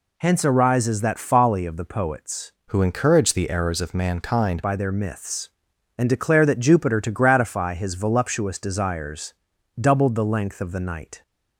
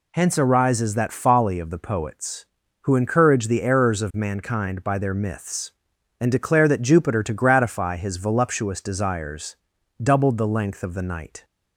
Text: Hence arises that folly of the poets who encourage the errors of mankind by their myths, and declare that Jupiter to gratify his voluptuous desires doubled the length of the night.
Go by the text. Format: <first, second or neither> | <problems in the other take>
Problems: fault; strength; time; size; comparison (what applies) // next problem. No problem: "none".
second | changes voice from "who" to "mankind"; from 2.6 to 4.6 s; 2.0 s long // pauses between "desires" and "doubled"; noticeable; at 9.3 s; 0.48 s long; noticeable in the second